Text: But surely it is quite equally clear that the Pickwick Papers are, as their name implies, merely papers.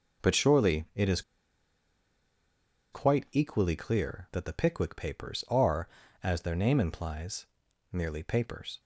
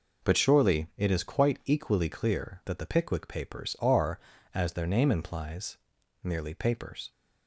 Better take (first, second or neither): second